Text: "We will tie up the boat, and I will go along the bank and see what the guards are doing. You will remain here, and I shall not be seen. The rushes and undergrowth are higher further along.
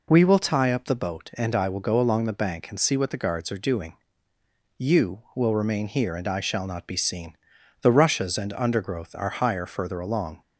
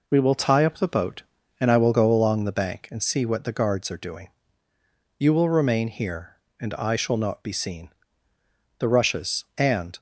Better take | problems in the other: first | stops before "undergrowth are higher further along"; at 9.9 s

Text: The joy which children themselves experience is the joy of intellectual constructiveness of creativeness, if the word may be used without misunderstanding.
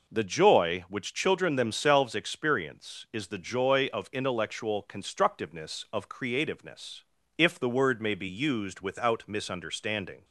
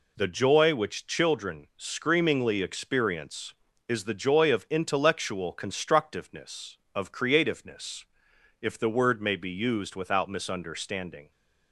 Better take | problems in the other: first | says "screamingly" for "themselves"; at 1.7 s

